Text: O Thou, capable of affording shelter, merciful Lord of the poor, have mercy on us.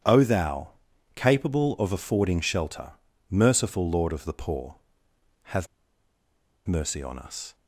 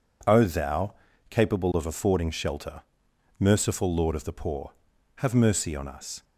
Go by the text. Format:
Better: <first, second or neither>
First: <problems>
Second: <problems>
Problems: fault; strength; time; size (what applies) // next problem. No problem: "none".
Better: second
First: starts louder than the rest; strong; until 1.4 s; 9.5 dB // pauses between "have" and "mercy"; at 5.6 s; 1.0 s long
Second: none